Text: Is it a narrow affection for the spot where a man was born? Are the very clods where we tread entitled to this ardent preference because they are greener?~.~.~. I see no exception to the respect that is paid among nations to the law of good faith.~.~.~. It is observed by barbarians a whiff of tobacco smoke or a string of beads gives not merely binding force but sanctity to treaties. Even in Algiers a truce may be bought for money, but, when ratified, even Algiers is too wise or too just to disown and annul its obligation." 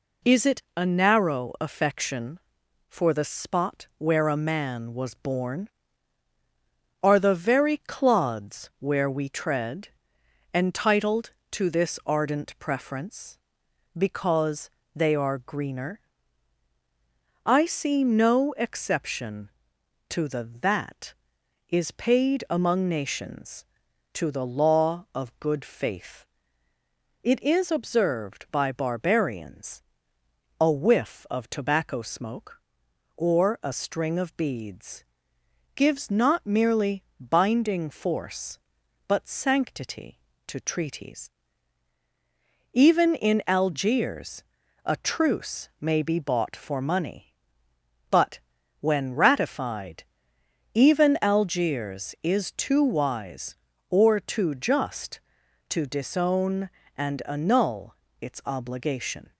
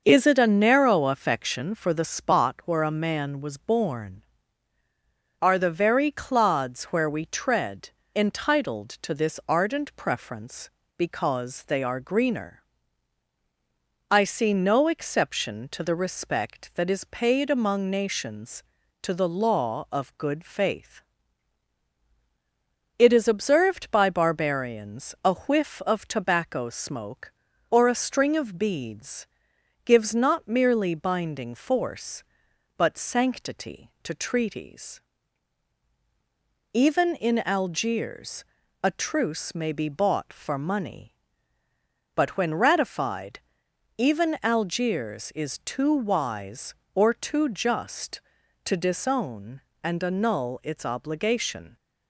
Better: second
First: pauses between "tread" and "entitled"; noticeable; at 9.8 s; 0.66 s long // pauses between "because" and "they"; slight; at 14.7 s; 0.24 s long // skips "respect"; at 20.5 s // pauses between "barbarians" and "a"; noticeable; at 29.8 s; 0.78 s long // pauses between "beads" and "gives"; noticeable; at 35.0 s; 0.72 s long // pauses between "merely" and "binding"; slight; at 37.0 s; 0.16 s long // pauses between "Algiers" and "a"; at 44.4 s; 0.40 s long // pauses between "annul" and "its"; slight; at 57.9 s; 0.24 s long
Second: pauses between "tread" and "entitled"; slight; at 7.9 s; 0.22 s long // pauses between "beads" and "gives"; noticeable; at 29.2 s; 0.58 s long // pauses between "Algiers" and "a"; slight; at 38.4 s; 0.36 s long

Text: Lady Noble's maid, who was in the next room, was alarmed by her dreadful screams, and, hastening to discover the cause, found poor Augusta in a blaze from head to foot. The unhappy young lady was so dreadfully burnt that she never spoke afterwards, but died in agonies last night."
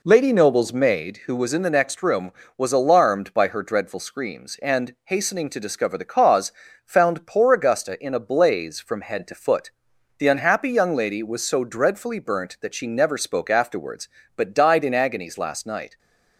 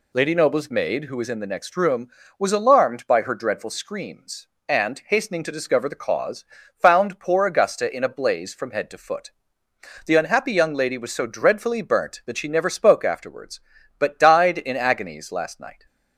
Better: second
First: starts louder than the rest; slight; until 1.4 s; 3 dB // stays silent after the last word; slight; from 15.8 s on; 0.5 s long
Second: none

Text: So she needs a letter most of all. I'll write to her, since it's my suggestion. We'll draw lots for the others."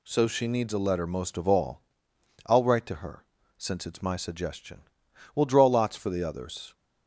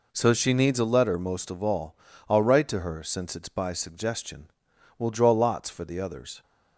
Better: first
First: none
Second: says "by" for "my"; at 3.4 s

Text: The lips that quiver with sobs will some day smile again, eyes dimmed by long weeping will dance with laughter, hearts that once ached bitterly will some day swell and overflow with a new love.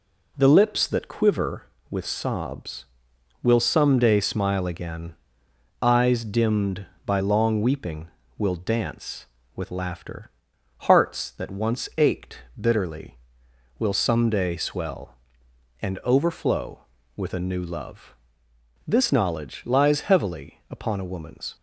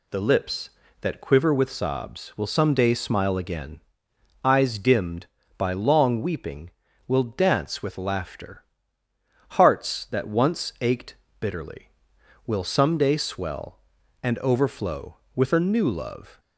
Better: second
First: pauses between "ached" and "bitterly"; slight; at 12.3 s; 0.22 s long // goes on to say "This knowledge lies heavily upon a woman's"; strong; from 18.8 s on; 2.6 s long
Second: pauses between "ached" and "bitterly"; slight; at 11.1 s; 0.26 s long

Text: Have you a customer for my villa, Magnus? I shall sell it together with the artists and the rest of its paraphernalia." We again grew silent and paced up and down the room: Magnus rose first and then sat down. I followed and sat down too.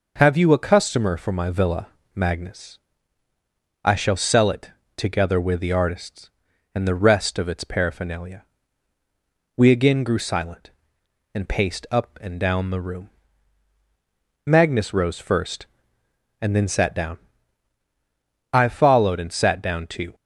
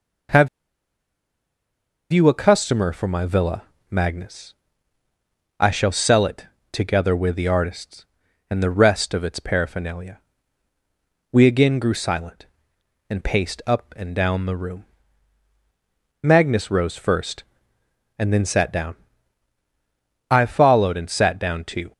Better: first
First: pauses between "it" and "together"; slight; at 4.7 s; 0.26 s long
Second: pauses between "Have" and "you"; strong; at 0.4 s; 1.6 s long // pauses between "it" and "together"; slight; at 6.4 s; 0.26 s long

